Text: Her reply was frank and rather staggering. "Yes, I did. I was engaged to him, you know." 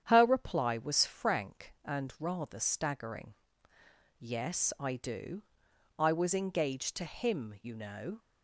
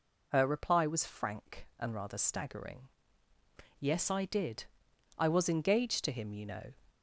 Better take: second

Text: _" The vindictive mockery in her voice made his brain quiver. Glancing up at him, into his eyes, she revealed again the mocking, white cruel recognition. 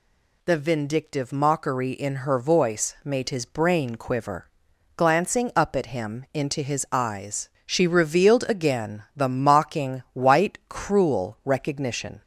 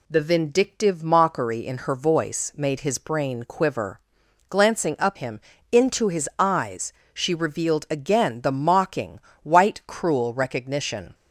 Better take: first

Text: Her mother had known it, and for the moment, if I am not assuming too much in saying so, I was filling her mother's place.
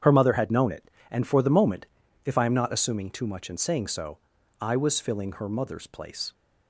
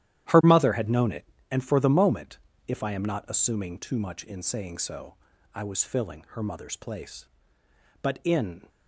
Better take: first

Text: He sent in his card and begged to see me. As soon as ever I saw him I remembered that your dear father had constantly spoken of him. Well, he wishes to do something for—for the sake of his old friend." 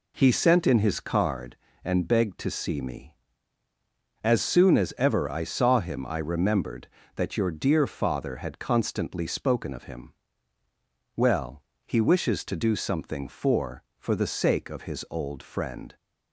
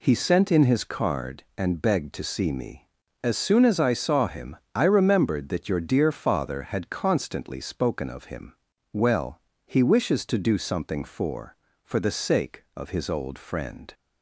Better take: first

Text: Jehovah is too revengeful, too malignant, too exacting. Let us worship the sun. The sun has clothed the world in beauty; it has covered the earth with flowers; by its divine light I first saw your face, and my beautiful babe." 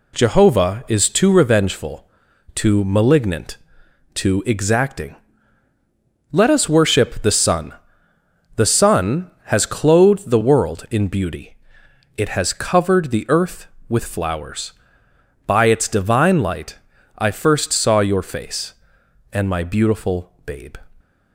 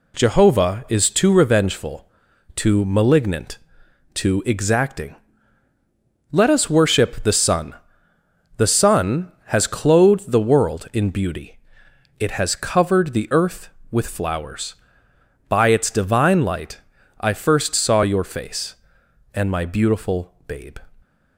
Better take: neither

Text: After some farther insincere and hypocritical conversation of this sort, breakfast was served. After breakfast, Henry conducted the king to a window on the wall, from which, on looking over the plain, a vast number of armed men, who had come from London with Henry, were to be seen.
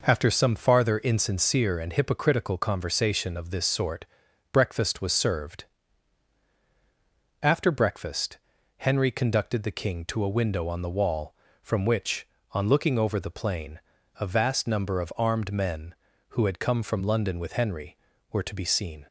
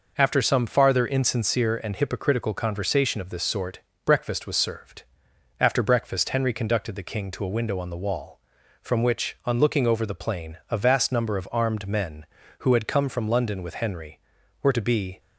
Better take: first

